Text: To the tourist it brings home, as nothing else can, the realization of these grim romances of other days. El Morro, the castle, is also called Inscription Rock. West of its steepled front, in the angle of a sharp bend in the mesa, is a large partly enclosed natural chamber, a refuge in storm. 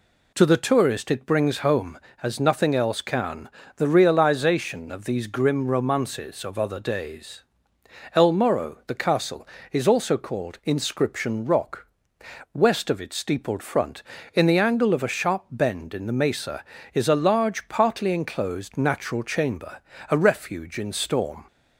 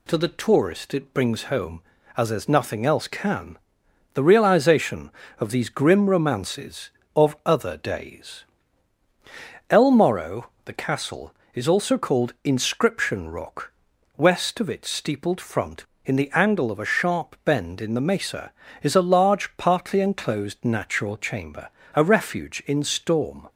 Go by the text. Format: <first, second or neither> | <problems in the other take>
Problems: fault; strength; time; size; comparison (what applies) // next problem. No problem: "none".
first | says "as" twice; at 2.3 s